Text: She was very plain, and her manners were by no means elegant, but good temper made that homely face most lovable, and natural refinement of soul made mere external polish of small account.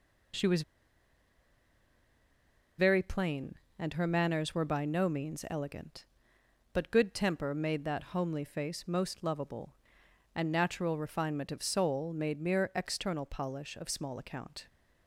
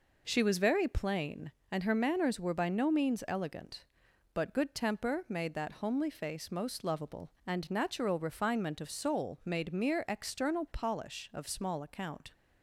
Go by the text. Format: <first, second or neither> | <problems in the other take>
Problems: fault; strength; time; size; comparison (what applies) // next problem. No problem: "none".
second | pauses between "was" and "very"; strong; at 0.6 s; 2.1 s long